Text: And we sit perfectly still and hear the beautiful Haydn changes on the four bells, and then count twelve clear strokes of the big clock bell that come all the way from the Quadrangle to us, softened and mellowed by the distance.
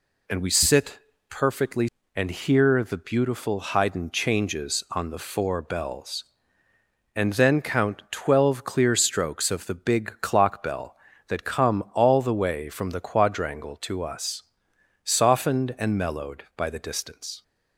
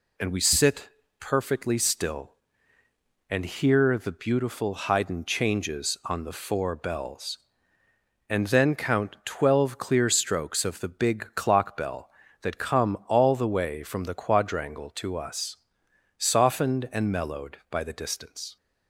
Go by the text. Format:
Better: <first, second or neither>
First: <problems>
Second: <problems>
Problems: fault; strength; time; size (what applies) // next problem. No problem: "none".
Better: second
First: pauses between "sit" and "perfectly"; slight; at 0.9 s; 0.30 s long // skips "still"; at 2.0 s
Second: pauses between "sit" and "perfectly"; slight; at 0.8 s; 0.30 s long